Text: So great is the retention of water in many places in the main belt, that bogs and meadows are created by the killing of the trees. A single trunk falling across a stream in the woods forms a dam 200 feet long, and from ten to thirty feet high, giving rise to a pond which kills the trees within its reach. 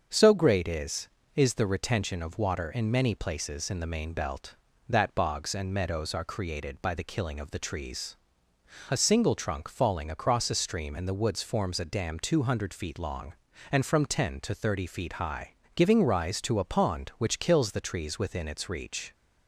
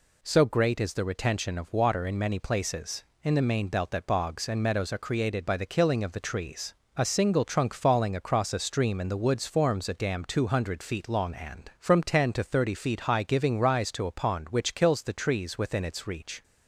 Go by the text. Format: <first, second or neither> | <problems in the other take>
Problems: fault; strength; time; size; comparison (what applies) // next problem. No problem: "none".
second | starts louder than the rest; until 1.3 s; 6.5 dB // says "is" twice; at 1.3 s